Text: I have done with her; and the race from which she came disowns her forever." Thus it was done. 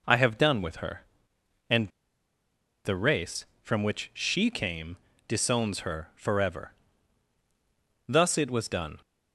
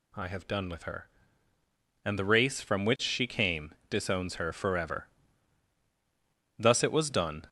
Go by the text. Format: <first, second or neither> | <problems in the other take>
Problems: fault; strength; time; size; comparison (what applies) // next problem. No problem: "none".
second | pauses between "and" and "the"; noticeable; at 1.8 s; 0.97 s long // pauses between "came" and "disowns"; slight; at 4.9 s; 0.32 s long; slight in the second